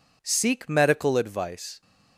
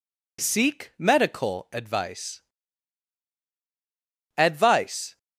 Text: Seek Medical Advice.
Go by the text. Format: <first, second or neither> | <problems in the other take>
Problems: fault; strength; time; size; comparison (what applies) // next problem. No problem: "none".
first | says "Advice" twice; at 4.3 s